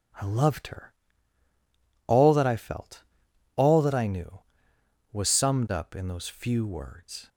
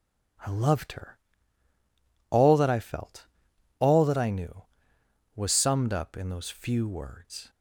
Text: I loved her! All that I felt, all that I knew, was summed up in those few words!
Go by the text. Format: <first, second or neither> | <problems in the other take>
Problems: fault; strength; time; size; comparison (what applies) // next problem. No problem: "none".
neither | none